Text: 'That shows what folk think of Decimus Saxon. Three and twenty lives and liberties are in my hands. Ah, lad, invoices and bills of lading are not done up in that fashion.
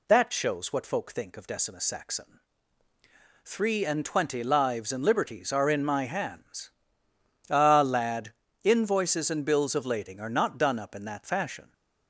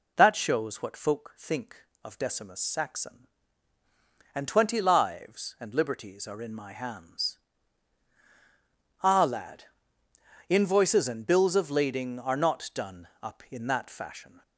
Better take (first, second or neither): first